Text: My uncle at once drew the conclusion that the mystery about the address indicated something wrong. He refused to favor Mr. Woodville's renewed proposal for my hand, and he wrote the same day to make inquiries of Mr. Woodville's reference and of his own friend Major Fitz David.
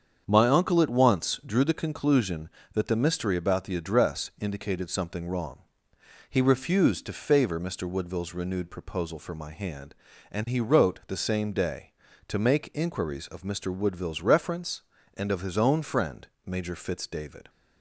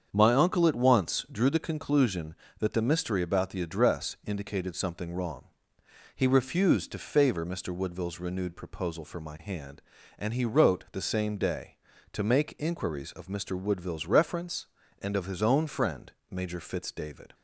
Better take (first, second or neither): neither